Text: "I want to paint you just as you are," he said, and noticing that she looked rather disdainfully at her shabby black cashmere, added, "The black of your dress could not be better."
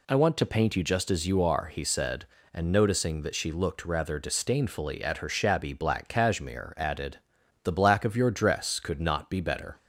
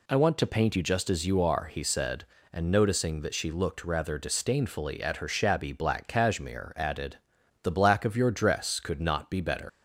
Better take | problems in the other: first | leaves "better" unfinished; at 9.6 s; 85 ms

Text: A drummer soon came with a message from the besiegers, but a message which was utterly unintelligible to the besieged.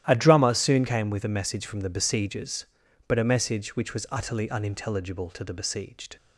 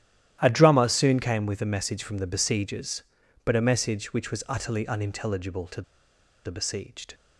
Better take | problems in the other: first | starts louder than the rest; strong; until 1.4 s; 12.5 dB; strong in the first // pauses between "to" and "the"; noticeable; at 5.8 s; 0.63 s long

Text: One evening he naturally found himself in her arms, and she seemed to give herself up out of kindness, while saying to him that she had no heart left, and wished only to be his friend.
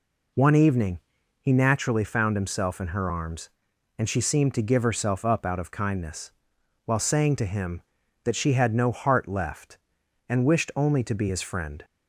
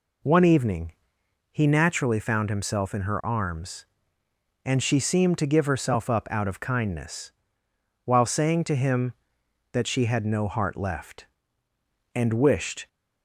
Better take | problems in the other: first | pauses between "evening" and "he"; noticeable; at 0.9 s; 0.58 s long; also in the first // stops before "only to be his friend"; at 12.8 s

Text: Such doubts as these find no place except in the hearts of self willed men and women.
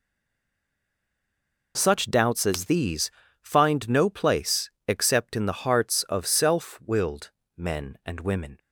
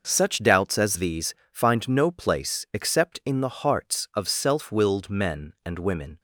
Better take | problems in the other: second | stays silent before the first word; noticeable; until 1.7 s; 1.7 s long // pauses between "these" and "find"; slight; at 3.1 s; 0.32 s long; slight in the second // pauses between "place" and "except"; slight; at 4.7 s; 0.18 s long // pauses between "willed" and "men"; slight; at 7.3 s; 0.26 s long

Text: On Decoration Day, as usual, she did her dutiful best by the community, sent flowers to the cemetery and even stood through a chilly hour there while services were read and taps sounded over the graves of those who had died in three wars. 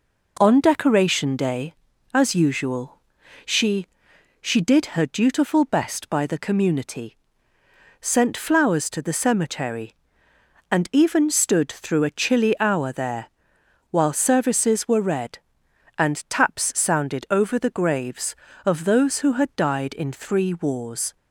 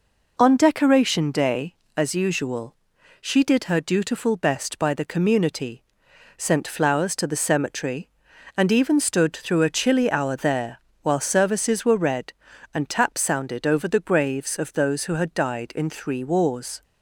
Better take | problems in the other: second | says "she" twice; at 4.3 s // pauses between "there" and "while"; noticeable; at 13.2 s; 0.60 s long; slight in the second

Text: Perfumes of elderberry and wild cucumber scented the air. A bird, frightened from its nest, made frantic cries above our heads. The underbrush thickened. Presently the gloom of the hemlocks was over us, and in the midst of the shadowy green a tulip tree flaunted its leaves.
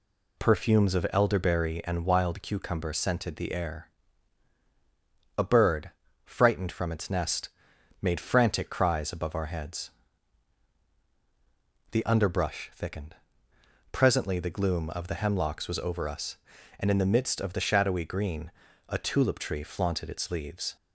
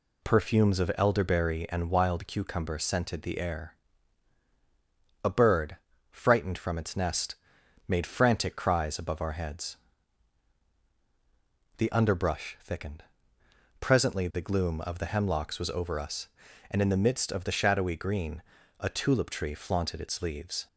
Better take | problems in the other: neither | pauses between "green" and "a"; the same in both

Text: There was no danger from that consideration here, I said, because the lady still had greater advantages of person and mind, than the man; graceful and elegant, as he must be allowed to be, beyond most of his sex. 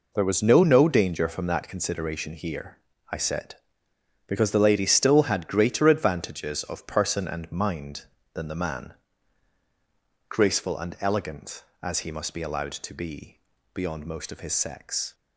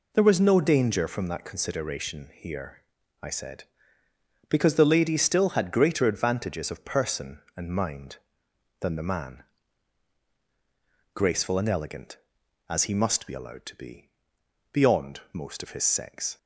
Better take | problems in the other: second | says "no" twice; at 0.6 s

